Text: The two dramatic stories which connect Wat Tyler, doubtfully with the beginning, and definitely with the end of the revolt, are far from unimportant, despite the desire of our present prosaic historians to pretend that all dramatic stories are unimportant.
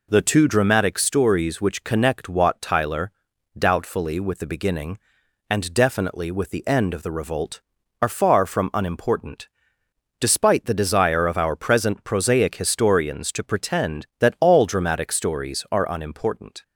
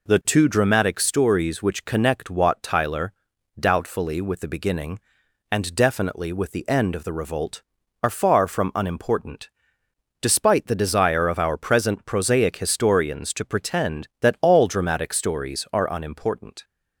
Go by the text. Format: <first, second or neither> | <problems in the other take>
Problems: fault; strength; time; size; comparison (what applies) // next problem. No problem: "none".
neither | none